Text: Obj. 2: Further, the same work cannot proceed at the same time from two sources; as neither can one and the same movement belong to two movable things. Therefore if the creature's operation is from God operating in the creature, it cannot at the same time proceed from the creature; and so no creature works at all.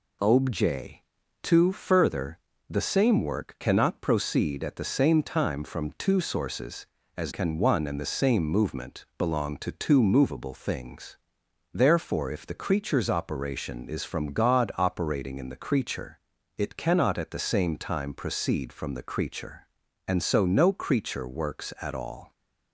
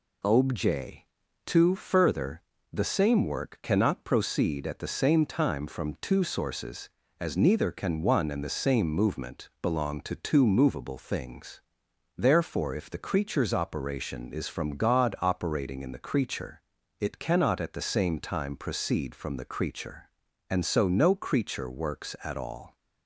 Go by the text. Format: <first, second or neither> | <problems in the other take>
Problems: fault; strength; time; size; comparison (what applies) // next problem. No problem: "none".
second | skips "neither"; at 7.3 s